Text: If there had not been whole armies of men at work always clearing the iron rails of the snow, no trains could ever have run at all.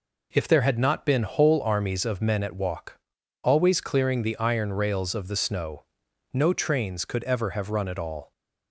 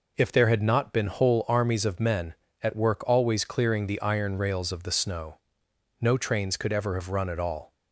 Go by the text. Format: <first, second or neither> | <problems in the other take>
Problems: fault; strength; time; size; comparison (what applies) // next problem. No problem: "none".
second | says "walk" for "work"; at 2.5 s